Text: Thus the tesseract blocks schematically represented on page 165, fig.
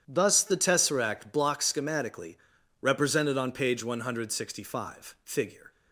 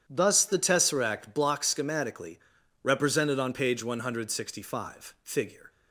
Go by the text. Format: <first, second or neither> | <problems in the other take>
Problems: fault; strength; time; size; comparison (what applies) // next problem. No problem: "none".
neither | starts louder than the rest; strong; the same in both // pauses between "schematically" and "represented"; the same in both